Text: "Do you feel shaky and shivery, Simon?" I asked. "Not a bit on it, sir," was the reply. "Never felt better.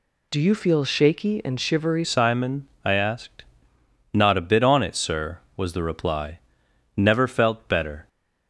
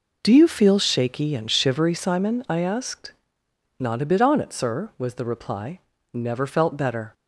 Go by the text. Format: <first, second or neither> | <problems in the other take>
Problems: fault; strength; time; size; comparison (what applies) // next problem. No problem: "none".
second | changes voice at "Simon"; from 2.0 s on; 6.0 s long